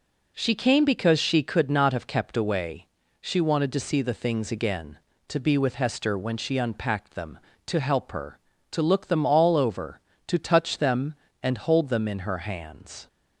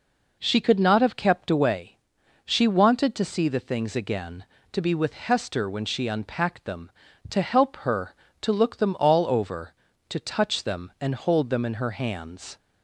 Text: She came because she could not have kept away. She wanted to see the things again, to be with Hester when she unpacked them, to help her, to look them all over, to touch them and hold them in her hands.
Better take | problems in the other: first | skips "came because she"; at 0.6 s

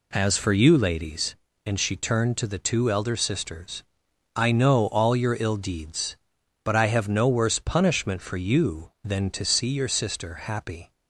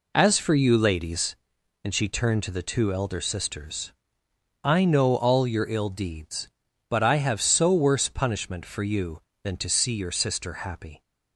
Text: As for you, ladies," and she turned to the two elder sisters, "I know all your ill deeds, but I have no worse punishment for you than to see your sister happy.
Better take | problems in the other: first | says "so" for "no"; at 7.4 s

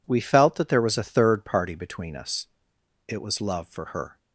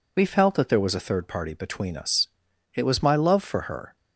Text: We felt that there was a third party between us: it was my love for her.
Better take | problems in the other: second | skips "my"; at 3.4 s

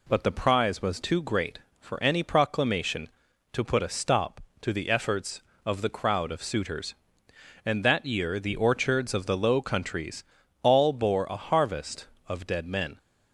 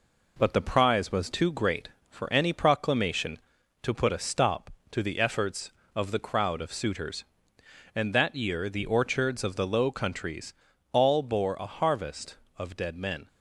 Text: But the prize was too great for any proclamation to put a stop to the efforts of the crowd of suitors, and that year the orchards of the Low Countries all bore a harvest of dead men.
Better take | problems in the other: first | gets quieter; slight; throughout; 3 dB // pauses between "Countries" and "all"; at 10.5 s; 0.38 s long; also in the first

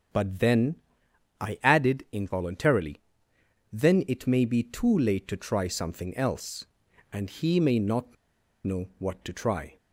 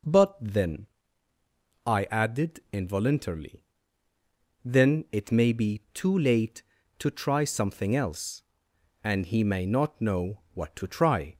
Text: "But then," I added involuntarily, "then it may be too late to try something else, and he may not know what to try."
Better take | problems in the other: second | starts louder than the rest; strong; until 1.8 s; 7.5 dB // pauses between "not" and "know"; noticeable; at 8.1 s; 0.50 s long

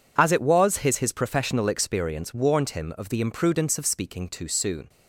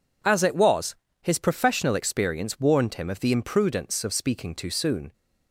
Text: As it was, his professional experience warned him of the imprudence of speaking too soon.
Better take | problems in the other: second | says "his" twice; at 0.9 s

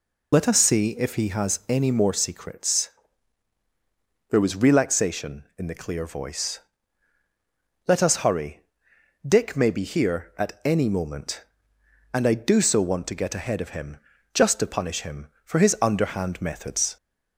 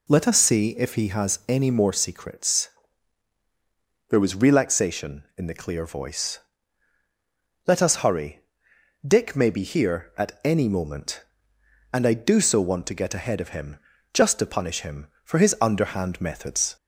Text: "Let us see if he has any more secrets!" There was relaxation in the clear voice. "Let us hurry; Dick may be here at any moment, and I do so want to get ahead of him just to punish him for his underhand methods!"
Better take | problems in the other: second | loses the start of "Let"; at 0.3 s; 30 ms // pauses between "him" and "just"; at 13.9 s; 0.38 s long; also in the second

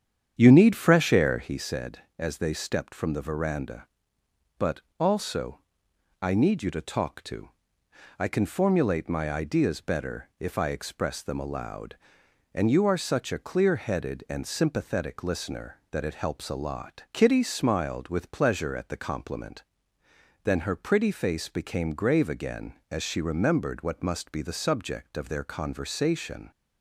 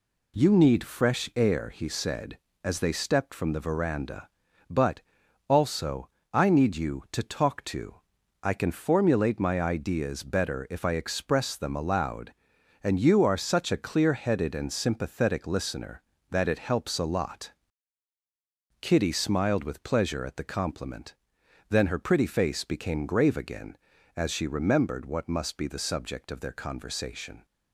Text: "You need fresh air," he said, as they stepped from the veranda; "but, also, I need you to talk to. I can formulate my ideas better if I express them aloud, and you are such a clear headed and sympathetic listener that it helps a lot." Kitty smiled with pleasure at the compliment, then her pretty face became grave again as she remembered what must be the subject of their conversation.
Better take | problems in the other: second | starts louder than the rest; strong; until 1.6 s; 8.5 dB

